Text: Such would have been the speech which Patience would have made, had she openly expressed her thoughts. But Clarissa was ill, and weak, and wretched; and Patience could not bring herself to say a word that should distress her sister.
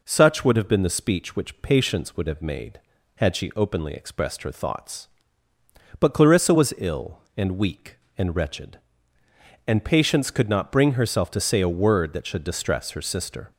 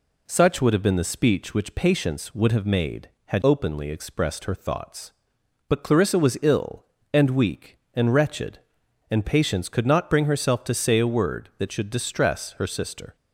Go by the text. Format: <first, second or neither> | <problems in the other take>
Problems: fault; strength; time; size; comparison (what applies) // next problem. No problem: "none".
first | skips "she"; at 3.4 s